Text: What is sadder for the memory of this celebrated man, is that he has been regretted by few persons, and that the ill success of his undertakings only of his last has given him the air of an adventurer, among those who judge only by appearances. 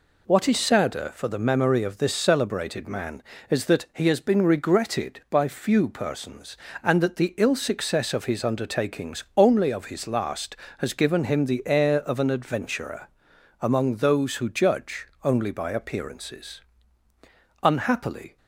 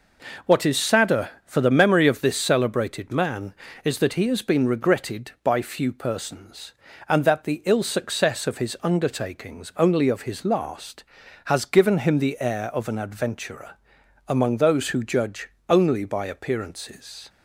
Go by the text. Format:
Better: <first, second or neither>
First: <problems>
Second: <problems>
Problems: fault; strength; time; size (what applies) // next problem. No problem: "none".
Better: second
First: pauses between "judge" and "only"; slight; at 15.0 s; 0.16 s long // goes on to say "Unhappily"; noticeable; from 17.6 s on; 0.74 s long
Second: pauses between "judge" and "only"; slight; at 15.5 s; 0.18 s long